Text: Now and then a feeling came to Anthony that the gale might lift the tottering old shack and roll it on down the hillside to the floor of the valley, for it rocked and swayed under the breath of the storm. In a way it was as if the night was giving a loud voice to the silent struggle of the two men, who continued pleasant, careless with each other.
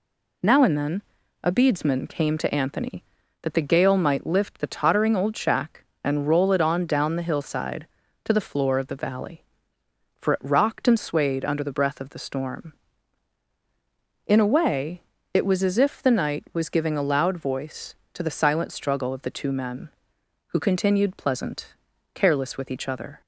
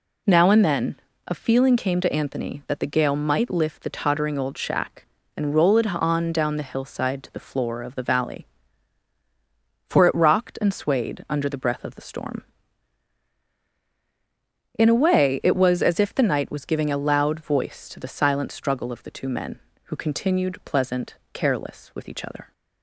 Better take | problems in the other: second | pauses between "then" and "a"; at 1.0 s; 0.40 s long; slight in the second // says "beadsman" for "feeling"; at 1.5 s // pauses between "way" and "it"; slight; at 15.0 s; 0.32 s long

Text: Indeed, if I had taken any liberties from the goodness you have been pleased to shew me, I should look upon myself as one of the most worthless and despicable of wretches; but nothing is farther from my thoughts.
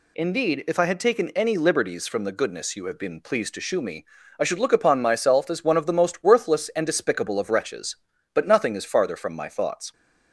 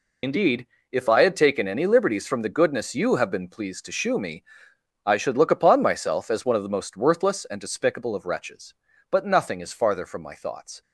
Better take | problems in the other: first | loses the start of "Indeed"; at 0.2 s; 60 ms

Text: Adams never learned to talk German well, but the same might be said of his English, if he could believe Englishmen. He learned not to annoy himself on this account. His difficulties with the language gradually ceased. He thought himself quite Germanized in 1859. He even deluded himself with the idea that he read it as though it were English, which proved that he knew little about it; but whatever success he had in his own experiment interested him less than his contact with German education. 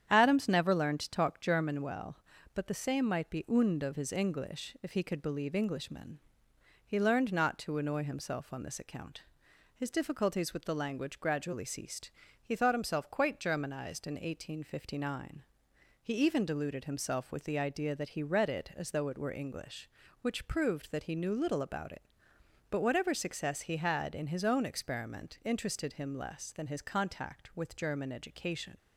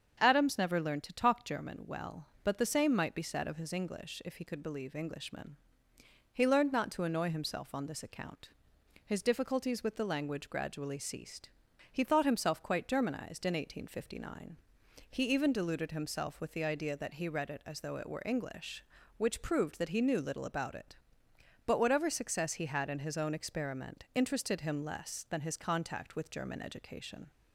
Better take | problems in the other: second | starts louder than the rest; strong; until 1.1 s; 9 dB; strong in the second // says "und" for "said"; at 3.4 s

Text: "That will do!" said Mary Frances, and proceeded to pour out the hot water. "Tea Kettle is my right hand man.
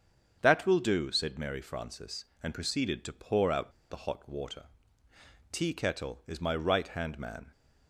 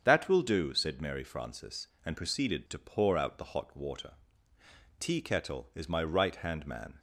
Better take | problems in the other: second | starts louder than the rest; strong; until 1.4 s; 7.5 dB; strong in the second // pauses between "out" and "the"; slight; at 3.7 s; 0.18 s long

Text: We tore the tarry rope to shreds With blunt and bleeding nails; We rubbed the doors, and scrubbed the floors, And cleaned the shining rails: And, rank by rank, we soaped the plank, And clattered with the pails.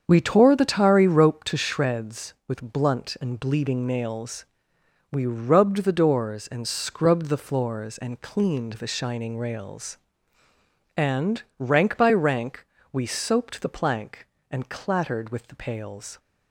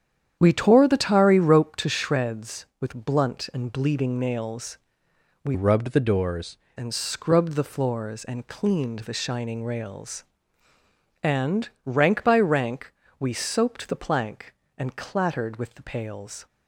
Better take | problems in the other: first | starts louder than the rest; strong; until 1.4 s; 9 dB; strong in the first // changes voice from "rubbed" to "doors"; from 5.5 to 6.5 s; 1.0 s long

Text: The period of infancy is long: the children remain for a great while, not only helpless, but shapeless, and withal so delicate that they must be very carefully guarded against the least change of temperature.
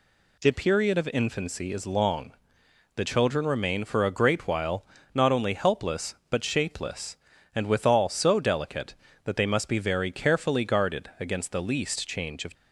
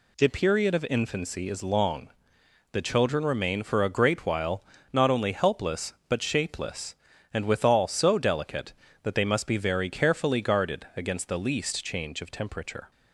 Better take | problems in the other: second | stops before "temperature"; at 12.5 s

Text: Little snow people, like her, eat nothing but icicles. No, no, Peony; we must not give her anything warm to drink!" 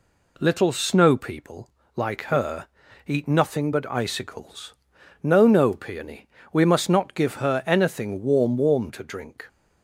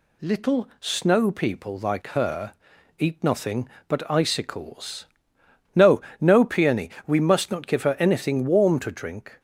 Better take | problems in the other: second | says "warm" twice; at 8.5 s

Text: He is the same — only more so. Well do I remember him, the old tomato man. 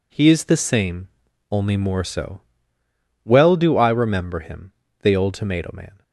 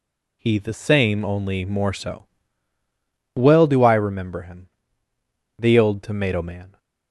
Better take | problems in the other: first | skips "is"; at 0.5 s

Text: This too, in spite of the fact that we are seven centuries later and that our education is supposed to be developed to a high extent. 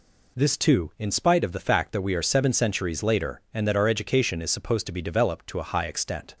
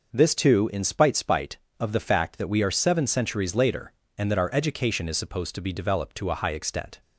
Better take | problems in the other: first | says "spite" twice; at 1.1 s

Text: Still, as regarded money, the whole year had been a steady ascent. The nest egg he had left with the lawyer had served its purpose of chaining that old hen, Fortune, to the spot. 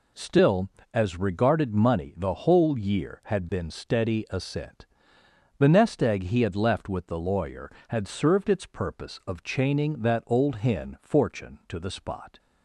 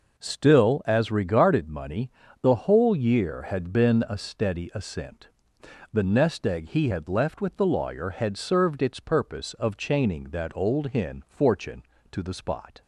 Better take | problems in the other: second | skips "a"; at 3.6 s

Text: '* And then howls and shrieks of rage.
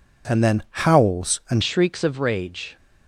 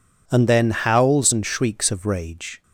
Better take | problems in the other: second | changes voice at "shrieks"; from 1.6 s on; 1.1 s long

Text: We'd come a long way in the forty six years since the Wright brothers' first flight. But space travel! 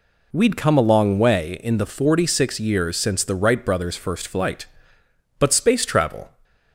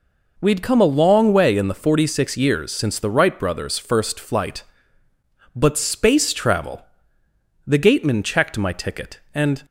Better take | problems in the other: first | goes on to say "The gateman checked my ticket and"; strong; from 7.6 s on; 1.9 s long

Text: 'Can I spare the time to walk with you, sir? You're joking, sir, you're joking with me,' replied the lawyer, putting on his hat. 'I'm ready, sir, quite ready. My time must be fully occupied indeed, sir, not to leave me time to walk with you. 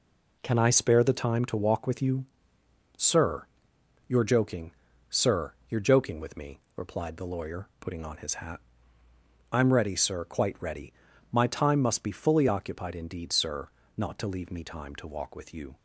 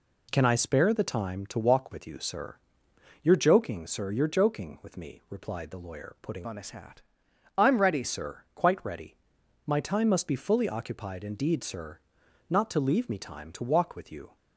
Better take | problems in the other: first | changes voice from "on" to "ready"; from 6.4 to 8.0 s; 1.6 s long

